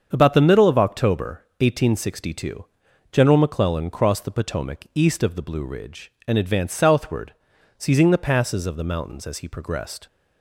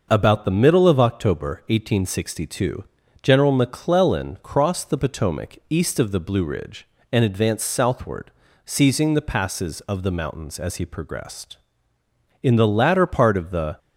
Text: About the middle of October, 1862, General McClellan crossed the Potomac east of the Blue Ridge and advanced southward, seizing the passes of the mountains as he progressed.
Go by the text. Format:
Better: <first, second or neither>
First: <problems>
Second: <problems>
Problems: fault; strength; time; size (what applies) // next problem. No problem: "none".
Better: first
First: starts louder than the rest; strong; until 1.1 s; 7 dB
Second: starts louder than the rest; noticeable; until 1.1 s; 6 dB // goes on to say "In the latter part of the"; from 12.4 s on; 1.3 s long